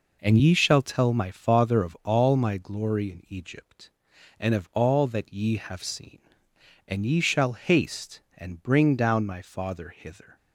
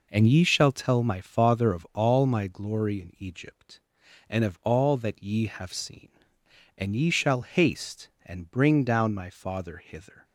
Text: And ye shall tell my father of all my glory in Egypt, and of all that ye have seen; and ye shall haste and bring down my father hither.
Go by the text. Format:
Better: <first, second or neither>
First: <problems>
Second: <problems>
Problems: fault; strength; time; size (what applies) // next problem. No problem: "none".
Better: neither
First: none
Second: none